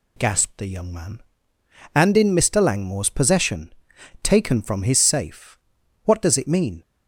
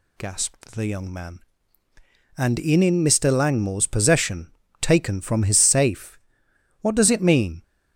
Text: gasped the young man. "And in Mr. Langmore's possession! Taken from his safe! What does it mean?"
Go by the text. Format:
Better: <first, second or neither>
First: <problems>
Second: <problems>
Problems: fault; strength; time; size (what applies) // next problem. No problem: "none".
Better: first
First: none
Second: says "in" twice; at 2.8 s